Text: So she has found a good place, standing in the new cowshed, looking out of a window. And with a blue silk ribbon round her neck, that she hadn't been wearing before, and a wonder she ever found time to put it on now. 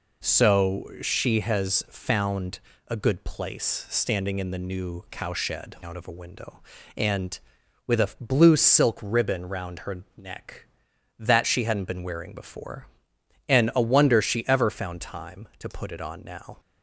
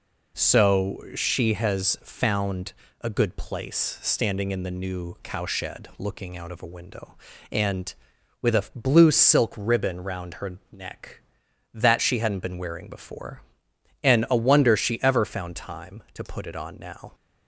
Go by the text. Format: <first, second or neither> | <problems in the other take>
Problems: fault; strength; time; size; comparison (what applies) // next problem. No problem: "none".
second | pauses between "found" and "a"; slight; at 2.6 s; 0.26 s long; slight in the second // skips "looking"; at 5.7 s